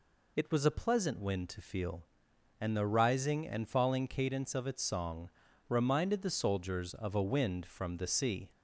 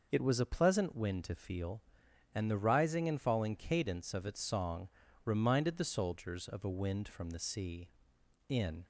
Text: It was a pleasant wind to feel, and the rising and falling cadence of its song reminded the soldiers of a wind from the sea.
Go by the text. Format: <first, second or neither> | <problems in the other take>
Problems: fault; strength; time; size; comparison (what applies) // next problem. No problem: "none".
first | pauses between "song" and "reminded"; slight; at 4.8 s; 0.36 s long; also in the first // goes on to say "In"; slight; from 8.4 s on; 0.38 s long